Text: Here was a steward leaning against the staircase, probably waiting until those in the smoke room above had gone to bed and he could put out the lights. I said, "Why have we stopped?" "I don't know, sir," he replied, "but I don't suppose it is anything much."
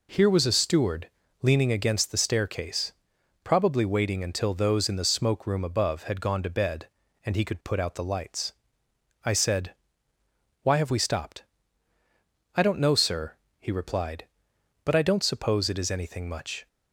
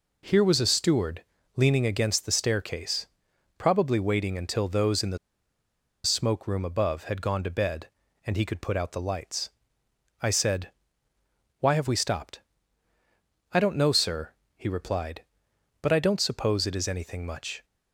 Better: first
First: pauses between "steward" and "leaning"; slight; at 1.0 s; 0.32 s long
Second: pauses between "steward" and "leaning"; slight; at 1.2 s; 0.32 s long // pauses between "the" and "smoke"; noticeable; at 5.1 s; 0.86 s long

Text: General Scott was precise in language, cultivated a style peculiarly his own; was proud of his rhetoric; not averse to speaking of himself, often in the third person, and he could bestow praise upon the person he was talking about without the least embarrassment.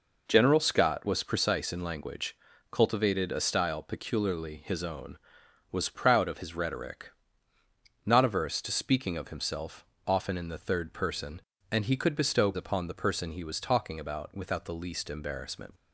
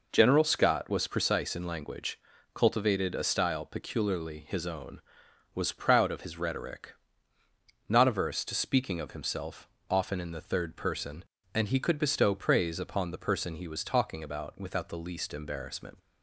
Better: second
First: skips "praise"; at 12.5 s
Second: none

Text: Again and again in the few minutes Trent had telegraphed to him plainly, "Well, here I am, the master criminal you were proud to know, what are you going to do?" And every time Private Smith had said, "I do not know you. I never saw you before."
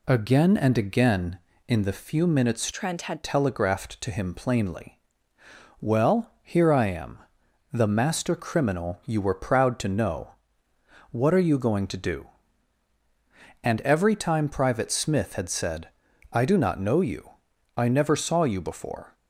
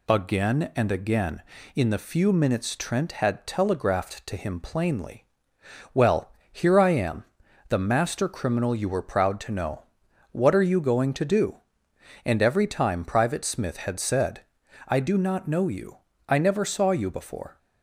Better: second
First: changes voice from "Trent" to "had"; from 2.7 to 3.2 s; 0.5 s long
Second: none

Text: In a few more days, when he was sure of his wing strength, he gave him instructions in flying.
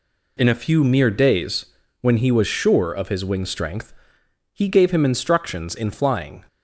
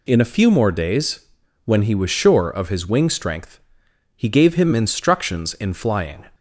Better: second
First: says "mere" for "more"; at 0.8 s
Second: none

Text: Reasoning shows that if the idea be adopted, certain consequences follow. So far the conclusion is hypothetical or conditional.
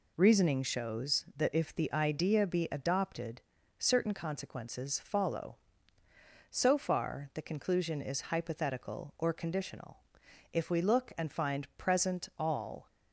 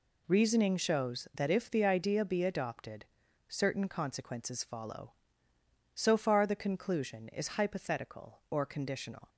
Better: second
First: goes on to say "If we look and find present all"; strong; from 10.5 s on; 2.3 s long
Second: none

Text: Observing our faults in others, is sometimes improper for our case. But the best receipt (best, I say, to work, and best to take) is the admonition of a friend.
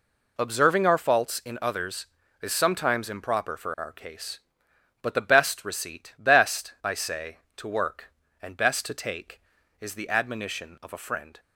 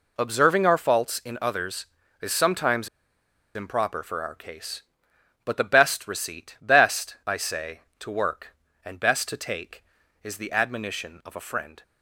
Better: first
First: none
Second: pauses between "sometimes" and "improper"; noticeable; at 2.8 s; 0.67 s long

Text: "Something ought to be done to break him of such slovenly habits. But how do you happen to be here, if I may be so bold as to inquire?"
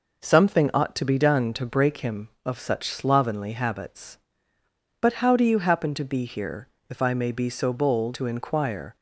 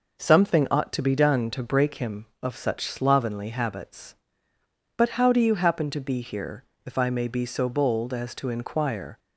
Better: second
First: skips "as"; at 8.1 s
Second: none

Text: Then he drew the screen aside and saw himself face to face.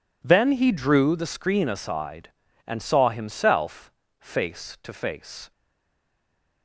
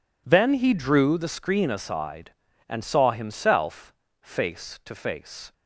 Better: second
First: pauses between "himself" and "face"; slight; at 3.9 s; 0.30 s long // stays silent after the last word; from 5.5 s on; 1.1 s long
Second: pauses between "himself" and "face"; slight; at 3.9 s; 0.30 s long

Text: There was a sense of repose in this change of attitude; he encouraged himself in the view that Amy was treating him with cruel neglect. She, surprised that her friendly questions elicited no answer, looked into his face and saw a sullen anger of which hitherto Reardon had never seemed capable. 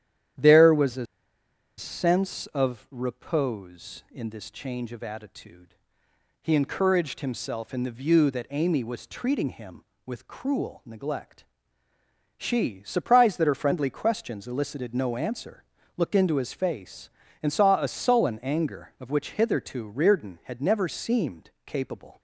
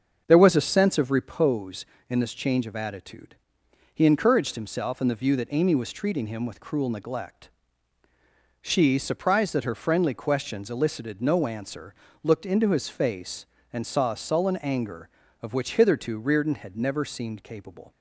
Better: second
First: starts louder than the rest; strong; until 2.1 s; 10.5 dB // pauses between "a" and "sense"; noticeable; at 1.0 s; 0.72 s long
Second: starts louder than the rest; until 1.2 s; 6.5 dB

